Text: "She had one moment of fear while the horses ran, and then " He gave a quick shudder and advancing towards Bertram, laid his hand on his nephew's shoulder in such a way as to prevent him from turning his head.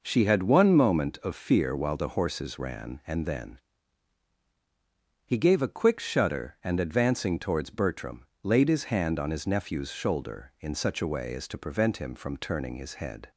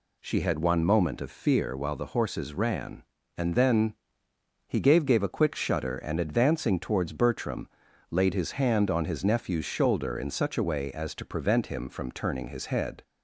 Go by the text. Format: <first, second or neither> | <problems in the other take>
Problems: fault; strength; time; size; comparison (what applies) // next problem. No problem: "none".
first | says "gave" twice; at 5.0 s